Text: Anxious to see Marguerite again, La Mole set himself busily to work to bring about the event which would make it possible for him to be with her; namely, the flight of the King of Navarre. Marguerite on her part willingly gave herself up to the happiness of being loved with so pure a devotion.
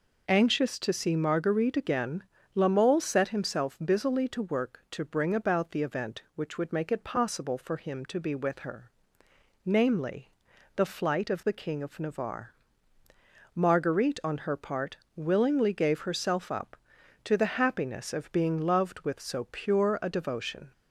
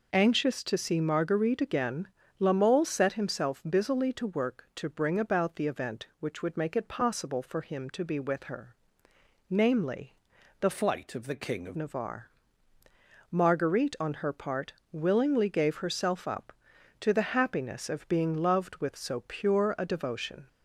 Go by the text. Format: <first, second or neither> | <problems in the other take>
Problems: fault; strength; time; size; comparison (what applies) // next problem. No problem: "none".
first | changes voice from "flight" to "of"; from 10.7 to 11.7 s; 1.0 s long // pauses between "part" and "willingly"; slight; at 14.7 s; 0.18 s long; slight in the first